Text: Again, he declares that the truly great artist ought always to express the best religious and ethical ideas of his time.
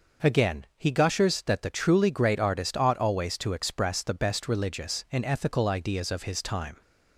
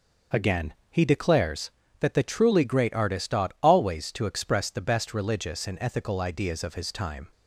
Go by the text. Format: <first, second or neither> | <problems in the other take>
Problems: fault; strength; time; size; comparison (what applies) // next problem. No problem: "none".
second | says "gushers" for "declares"; at 0.9 s